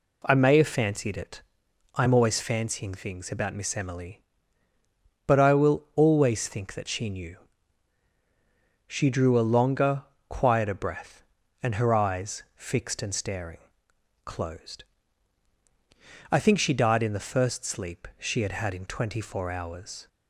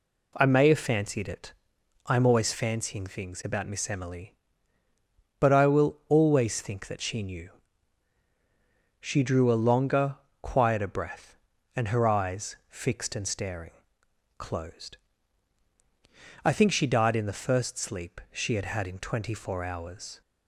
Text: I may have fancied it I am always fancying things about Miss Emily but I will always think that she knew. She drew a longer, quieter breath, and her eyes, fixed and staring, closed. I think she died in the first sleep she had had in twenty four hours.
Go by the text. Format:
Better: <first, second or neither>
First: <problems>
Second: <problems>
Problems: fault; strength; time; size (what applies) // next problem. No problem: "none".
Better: neither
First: pauses between "it" and "I"; noticeable; at 1.4 s; 0.54 s long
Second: pauses between "it" and "I"; noticeable; at 1.5 s; 0.54 s long